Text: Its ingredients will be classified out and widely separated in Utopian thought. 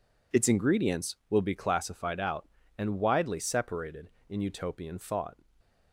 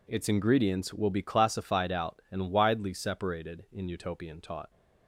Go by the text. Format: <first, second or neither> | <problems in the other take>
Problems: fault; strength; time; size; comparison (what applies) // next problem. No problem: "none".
first | says "taught" for "thought"; at 4.3 s